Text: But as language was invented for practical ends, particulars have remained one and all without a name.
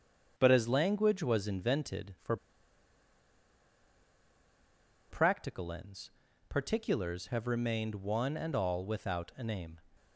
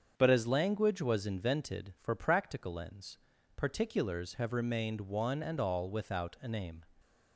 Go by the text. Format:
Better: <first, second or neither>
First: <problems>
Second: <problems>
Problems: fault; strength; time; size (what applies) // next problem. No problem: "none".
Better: second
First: starts louder than the rest; strong; until 1.3 s; 7 dB // pauses between "for" and "practical"; strong; at 2.3 s; 2.7 s long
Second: starts louder than the rest; until 1.1 s; 7 dB